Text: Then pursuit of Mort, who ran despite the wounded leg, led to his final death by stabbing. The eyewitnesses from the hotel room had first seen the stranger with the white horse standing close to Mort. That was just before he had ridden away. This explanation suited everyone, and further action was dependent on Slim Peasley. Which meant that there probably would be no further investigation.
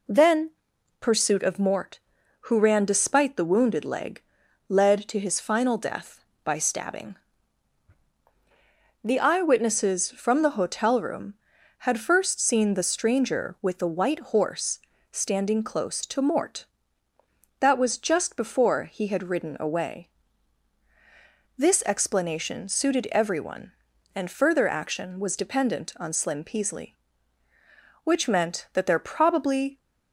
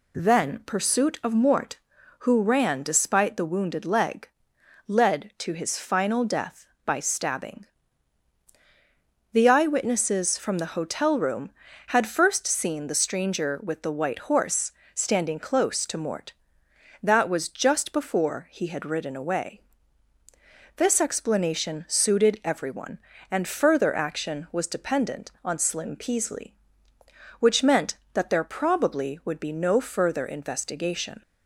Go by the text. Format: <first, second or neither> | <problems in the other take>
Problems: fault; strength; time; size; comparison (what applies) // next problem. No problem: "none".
second | pauses between "Then" and "pursuit"; noticeable; at 0.5 s; 0.50 s long // pauses between "horse" and "standing"; slight; at 14.7 s; 0.32 s long; slight in the second // stops before "would be no further investigation"; at 29.7 s